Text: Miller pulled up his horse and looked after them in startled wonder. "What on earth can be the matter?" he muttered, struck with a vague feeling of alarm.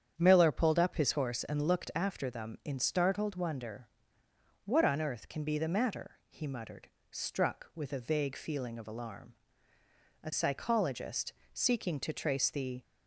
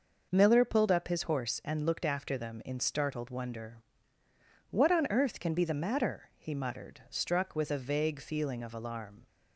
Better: second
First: starts louder than the rest; strong; until 1.1 s; 8.5 dB // goes on to say "A psychologist seeking to trace the"; strong; from 10.2 s on; 2.5 s long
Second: none

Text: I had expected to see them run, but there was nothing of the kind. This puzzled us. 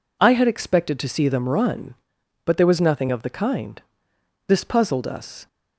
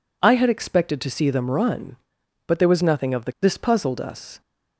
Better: first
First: none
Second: skips "kind"; at 3.3 s

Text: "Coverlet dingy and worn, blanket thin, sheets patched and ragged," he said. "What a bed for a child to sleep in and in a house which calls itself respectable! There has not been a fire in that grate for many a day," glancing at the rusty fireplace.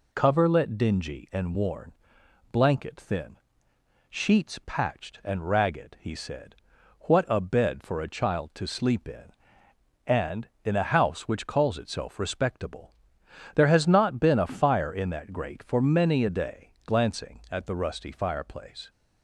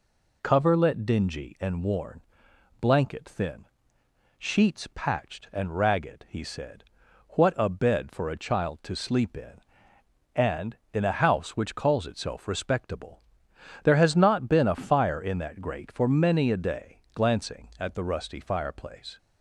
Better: neither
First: none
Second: none

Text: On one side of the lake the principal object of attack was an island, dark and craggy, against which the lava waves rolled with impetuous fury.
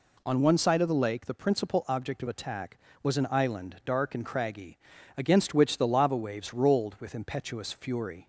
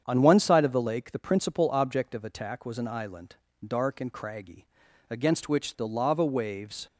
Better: first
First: none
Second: starts louder than the rest; strong; until 1.0 s; 8 dB // stops before "rolled with impetuous fury"; at 6.8 s

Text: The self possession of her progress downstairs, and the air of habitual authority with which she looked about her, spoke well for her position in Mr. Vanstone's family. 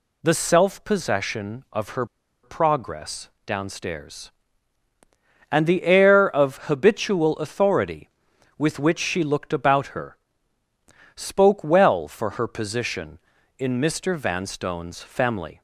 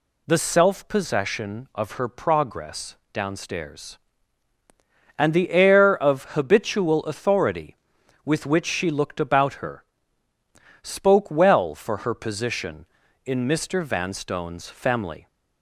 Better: second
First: pauses between "her" and "progress"; at 2.0 s; 0.37 s long // pauses between "progress" and "downstairs"; slight; at 3.2 s; 0.16 s long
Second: pauses between "progress" and "downstairs"; slight; at 2.9 s; 0.16 s long

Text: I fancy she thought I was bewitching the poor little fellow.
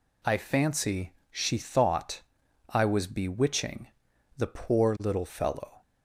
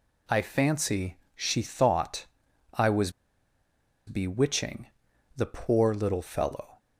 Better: first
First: pauses between "fancy" and "she"; slight; at 1.1 s; 0.20 s long // pauses between "thought" and "I"; noticeable; at 2.2 s; 0.48 s long // pauses between "bewitching" and "the"; noticeable; at 3.8 s; 0.50 s long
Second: pauses between "fancy" and "she"; slight; at 1.1 s; 0.20 s long // pauses between "thought" and "I"; noticeable; at 2.2 s; 0.48 s long // pauses between "was" and "bewitching"; noticeable; at 3.1 s; 0.95 s long // pauses between "bewitching" and "the"; noticeable; at 4.8 s; 0.50 s long

